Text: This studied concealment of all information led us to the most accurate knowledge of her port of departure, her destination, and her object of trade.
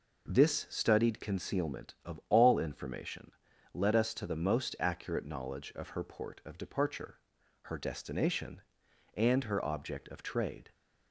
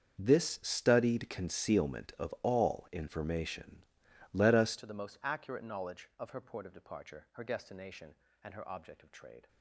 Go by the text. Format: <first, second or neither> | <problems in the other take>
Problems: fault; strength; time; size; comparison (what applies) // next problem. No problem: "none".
first | starts louder than the rest; until 1.2 s; 7 dB // pauses between "information" and "led"; noticeable; at 3.8 s; 0.50 s long; also in the first // changes voice at "to"; from 4.7 s on; 4.7 s long